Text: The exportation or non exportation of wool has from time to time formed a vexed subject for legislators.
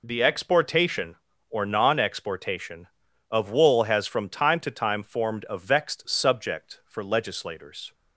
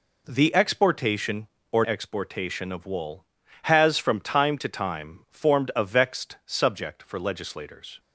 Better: first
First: none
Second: skips "non"; at 1.8 s

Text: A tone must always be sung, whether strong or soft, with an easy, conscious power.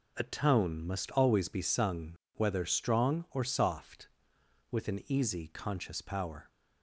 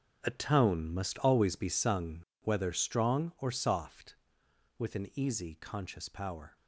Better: first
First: none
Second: gets quieter; strong; throughout; 12 dB

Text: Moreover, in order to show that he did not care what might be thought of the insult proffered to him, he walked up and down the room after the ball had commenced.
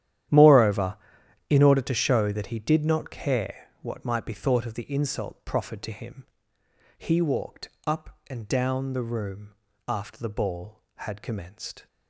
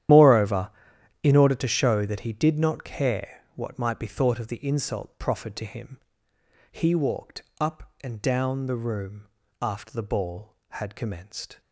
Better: first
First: starts louder than the rest; strong; until 1.8 s; 11.5 dB // pauses between "walked" and "up"; slight; at 7.6 s; 0.18 s long // pauses between "room" and "after"; slight; at 9.5 s; 0.34 s long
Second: loses the start of "Moreover"; at 0.0 s; 55 ms // starts louder than the rest; strong; until 1.6 s; 11.5 dB // pauses between "walked" and "up"; slight; at 7.4 s; 0.18 s long // pauses between "room" and "after"; slight; at 9.2 s; 0.34 s long

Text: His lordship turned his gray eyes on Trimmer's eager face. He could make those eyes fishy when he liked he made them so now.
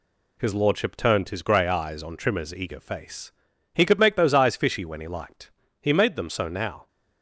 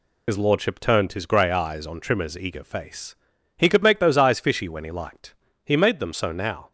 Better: first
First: pauses between "liked" and "he"; slight; at 5.5 s; 0.28 s long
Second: loses the start of "His"; at 0.2 s; 50 ms // pauses between "liked" and "he"; slight; at 5.3 s; 0.28 s long

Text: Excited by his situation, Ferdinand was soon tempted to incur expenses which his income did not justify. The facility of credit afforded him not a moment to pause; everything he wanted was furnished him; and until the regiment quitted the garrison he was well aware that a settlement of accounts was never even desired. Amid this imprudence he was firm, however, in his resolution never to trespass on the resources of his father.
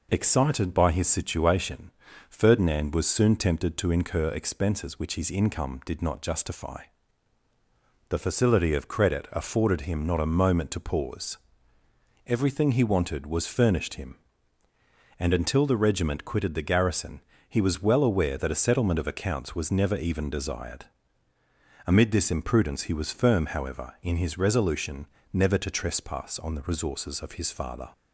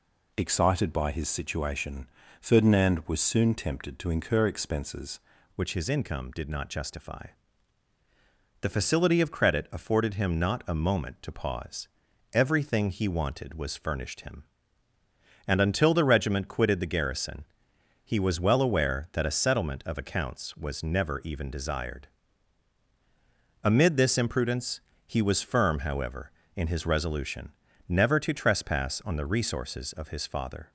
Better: first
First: pauses between "garrison" and "he"; slight; at 17.1 s; 0.28 s long // pauses between "resolution" and "never"; slight; at 25.0 s; 0.26 s long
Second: changes voice at "which"; from 5.5 s on; 25.2 s long // pauses between "garrison" and "he"; noticeable; at 17.4 s; 0.60 s long // pauses between "imprudence" and "he"; slight; at 24.7 s; 0.26 s long // pauses between "resolution" and "never"; slight; at 27.5 s; 0.36 s long

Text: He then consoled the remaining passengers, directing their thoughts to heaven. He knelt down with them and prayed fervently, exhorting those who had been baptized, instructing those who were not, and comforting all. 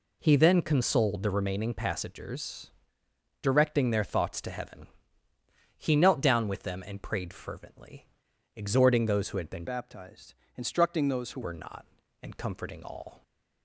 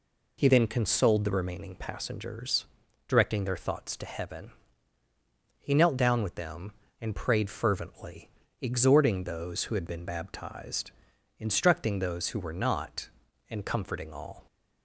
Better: second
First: changes voice from "baptized" to "who"; from 9.6 to 11.4 s; 1.8 s long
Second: none

